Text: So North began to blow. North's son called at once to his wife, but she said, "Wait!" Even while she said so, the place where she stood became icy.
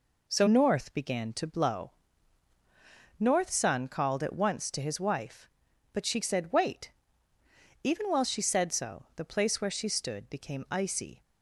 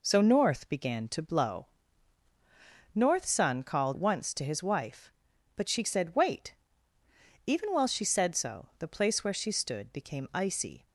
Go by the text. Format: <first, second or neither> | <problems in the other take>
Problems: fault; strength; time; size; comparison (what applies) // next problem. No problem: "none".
first | skips "at"; at 3.9 s